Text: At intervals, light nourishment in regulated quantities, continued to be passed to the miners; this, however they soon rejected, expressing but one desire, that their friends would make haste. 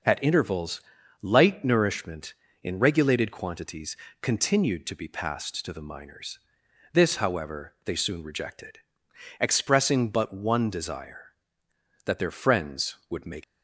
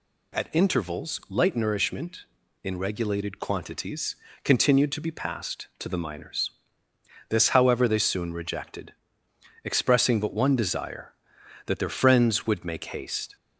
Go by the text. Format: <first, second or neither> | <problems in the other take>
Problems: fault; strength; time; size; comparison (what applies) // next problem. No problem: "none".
second | stops before "haste"; at 13.4 s